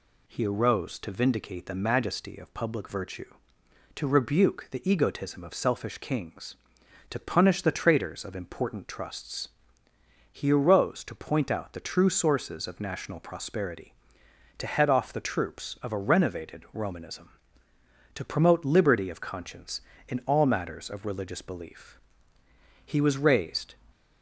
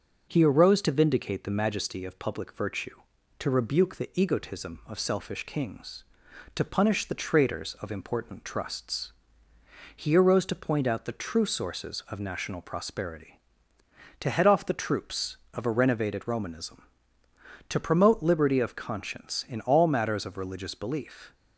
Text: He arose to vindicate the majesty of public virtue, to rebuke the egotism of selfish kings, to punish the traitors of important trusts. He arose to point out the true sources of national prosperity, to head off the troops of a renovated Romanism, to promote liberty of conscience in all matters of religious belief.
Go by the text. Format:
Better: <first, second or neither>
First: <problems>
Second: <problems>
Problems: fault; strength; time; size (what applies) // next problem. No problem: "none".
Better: second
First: goes on to say "He was raised"; noticeable; from 22.8 s on; 0.90 s long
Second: none